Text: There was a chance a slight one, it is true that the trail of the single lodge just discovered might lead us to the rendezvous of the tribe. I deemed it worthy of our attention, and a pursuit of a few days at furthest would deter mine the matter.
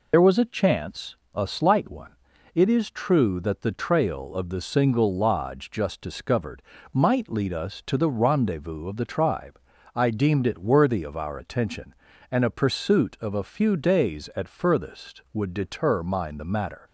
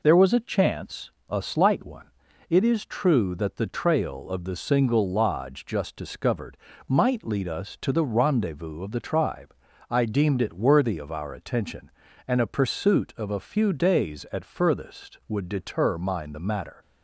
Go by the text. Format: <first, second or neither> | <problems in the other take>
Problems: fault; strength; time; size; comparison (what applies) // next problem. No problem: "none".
second | loses the start of "There"; at 0.1 s; 55 ms // pauses between "chance" and "a"; slight; at 1.1 s; 0.18 s long; slight in the second // pauses between "discovered" and "might"; slight; at 6.6 s; 0.32 s long; slight in the second